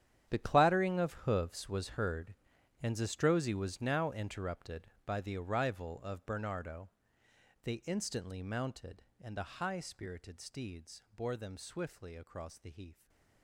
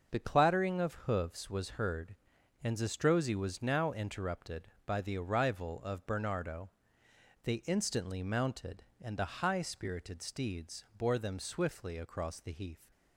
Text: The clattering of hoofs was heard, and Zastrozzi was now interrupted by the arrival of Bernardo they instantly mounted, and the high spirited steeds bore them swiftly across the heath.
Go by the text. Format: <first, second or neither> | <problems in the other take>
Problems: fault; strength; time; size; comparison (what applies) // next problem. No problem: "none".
second | gets quieter; strong; throughout; 15.5 dB // starts louder than the rest; strong; until 1.3 s; 9.5 dB; also in the second // pauses between "Bernardo" and "they"; noticeable; at 6.8 s; 0.74 s long; noticeable in the second // stays silent after the last word; slight; from 12.9 s on; 0.5 s long